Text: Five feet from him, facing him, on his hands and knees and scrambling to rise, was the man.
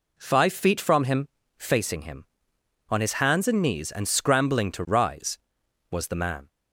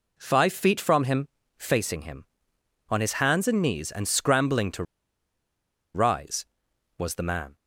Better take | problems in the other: first | pauses between "to" and "rise"; at 4.8 s; 1.1 s long

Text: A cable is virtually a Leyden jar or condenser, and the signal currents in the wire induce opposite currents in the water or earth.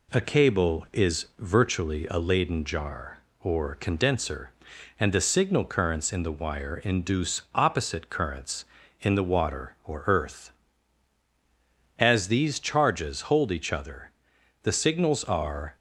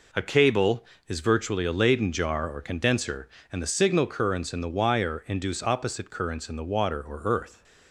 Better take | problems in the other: second | goes on to say "As these charges hold each other the signals are"; strong; from 11.9 s on; 3.7 s long

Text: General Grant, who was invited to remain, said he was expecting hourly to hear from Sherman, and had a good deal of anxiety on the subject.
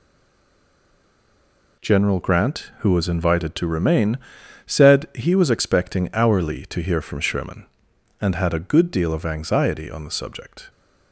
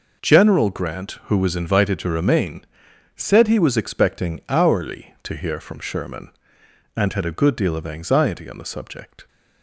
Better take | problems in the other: second | stays silent before the first word; noticeable; until 1.7 s; 1.7 s long

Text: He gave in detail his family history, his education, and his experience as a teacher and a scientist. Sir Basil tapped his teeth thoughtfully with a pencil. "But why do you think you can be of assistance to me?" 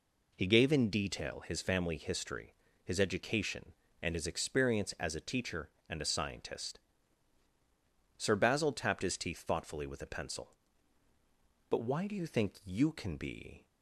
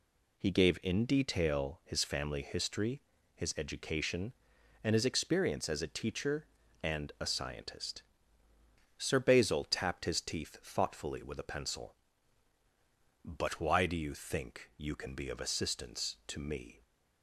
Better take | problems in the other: second | stops before "of assistance to me"; at 13.6 s

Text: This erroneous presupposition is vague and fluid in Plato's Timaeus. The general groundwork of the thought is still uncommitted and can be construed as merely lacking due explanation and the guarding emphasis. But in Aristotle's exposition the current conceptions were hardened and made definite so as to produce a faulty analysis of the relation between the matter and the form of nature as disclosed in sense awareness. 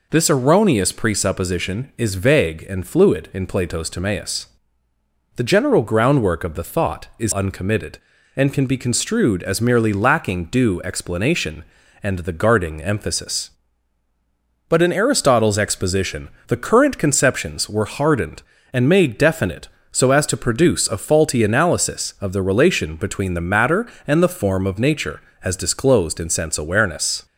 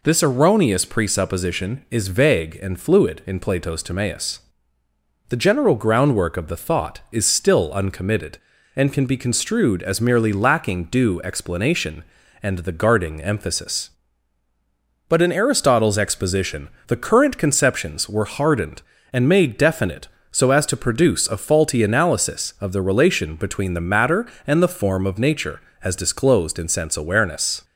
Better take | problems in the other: second | skips "still"; at 7.3 s // pauses between "exposition" and "the"; slight; at 16.2 s; 0.18 s long; slight in the second

